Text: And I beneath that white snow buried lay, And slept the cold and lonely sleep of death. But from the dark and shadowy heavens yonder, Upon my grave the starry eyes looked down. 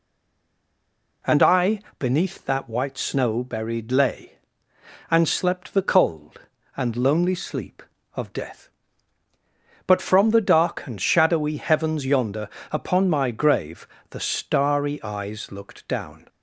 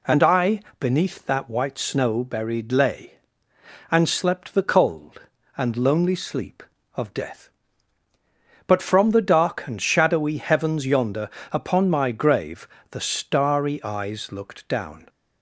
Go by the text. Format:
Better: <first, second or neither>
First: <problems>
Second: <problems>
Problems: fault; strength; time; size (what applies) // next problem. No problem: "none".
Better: second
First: stays silent before the first word; noticeable; until 1.2 s; 1.2 s long // pauses between "I" and "beneath"; slight; at 1.7 s; 0.20 s long // pauses between "grave" and "the"; slight; at 13.8 s; 0.22 s long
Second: pauses between "I" and "beneath"; slight; at 0.5 s; 0.20 s long // pauses between "grave" and "the"; slight; at 12.6 s; 0.22 s long